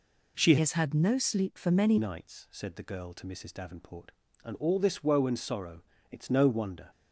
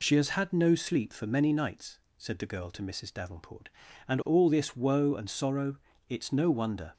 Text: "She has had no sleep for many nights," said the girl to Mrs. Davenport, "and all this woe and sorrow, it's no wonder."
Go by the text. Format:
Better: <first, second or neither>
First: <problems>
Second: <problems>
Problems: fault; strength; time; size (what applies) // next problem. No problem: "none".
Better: second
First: changes voice from "has" to "many"; from 0.5 to 1.9 s; 1.4 s long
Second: none